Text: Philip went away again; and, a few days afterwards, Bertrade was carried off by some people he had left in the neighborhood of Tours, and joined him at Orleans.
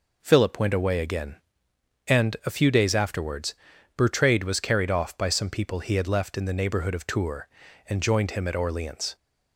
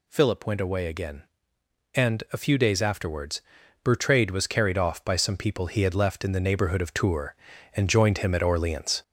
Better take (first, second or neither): first